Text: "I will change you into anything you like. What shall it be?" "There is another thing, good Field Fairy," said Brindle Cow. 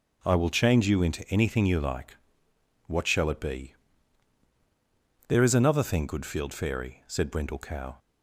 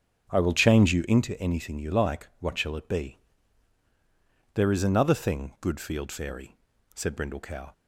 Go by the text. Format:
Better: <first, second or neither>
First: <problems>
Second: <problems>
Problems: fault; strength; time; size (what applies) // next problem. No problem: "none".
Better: first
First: none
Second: starts louder than the rest; strong; until 1.2 s; 7.5 dB